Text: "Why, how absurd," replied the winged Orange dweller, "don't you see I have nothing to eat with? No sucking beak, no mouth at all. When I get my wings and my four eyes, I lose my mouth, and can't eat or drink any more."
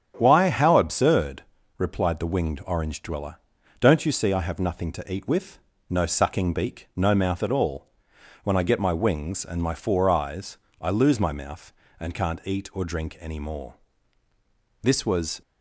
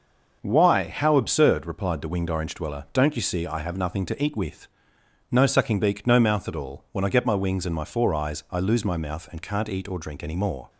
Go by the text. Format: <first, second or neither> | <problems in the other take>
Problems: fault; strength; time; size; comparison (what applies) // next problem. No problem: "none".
second | starts louder than the rest; strong; until 1.1 s; 8.5 dB; also in the second // goes on to say "This was"; from 14.8 s on; 0.60 s long